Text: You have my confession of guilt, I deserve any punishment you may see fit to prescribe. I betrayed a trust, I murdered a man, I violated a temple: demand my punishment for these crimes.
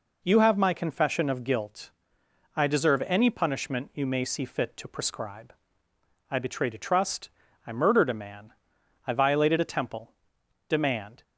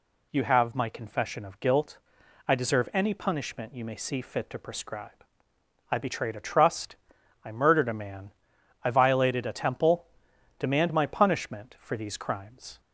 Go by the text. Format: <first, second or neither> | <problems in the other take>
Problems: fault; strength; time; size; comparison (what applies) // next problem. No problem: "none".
second | stops before "my punishment for these crimes"; at 11.2 s